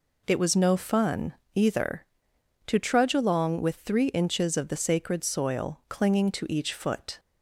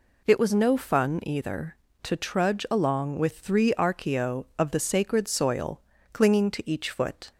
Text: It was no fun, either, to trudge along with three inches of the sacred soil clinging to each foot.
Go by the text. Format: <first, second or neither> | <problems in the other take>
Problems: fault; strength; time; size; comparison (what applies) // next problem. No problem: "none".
first | says "archaeo" for "inches"; at 3.7 s // pauses between "soil" and "clinging"; slight; at 5.8 s; 0.32 s long